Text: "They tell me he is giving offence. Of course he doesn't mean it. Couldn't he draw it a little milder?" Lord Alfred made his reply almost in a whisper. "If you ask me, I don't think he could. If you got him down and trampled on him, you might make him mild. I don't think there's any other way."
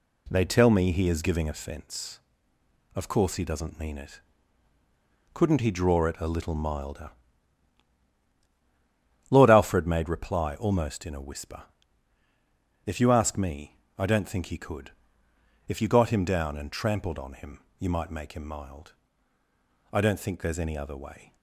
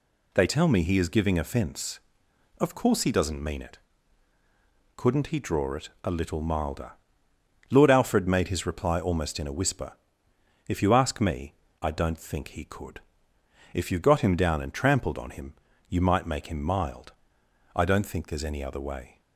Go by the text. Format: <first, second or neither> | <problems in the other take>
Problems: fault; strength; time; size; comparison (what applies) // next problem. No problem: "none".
second | skips "his"; at 10.0 s